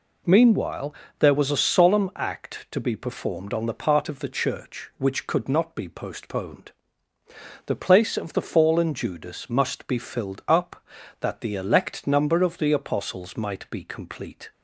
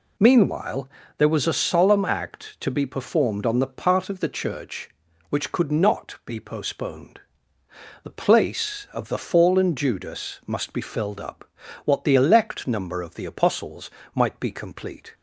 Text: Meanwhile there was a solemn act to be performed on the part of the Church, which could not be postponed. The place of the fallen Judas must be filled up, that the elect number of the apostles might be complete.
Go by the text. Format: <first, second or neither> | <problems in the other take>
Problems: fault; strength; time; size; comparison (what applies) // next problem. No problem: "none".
first | pauses between "Meanwhile" and "there"; slight; at 0.8 s; 0.30 s long; slight in the first // says "what" for "that"; at 11.8 s // pauses between "apostles" and "might"; slight; at 13.8 s; 0.24 s long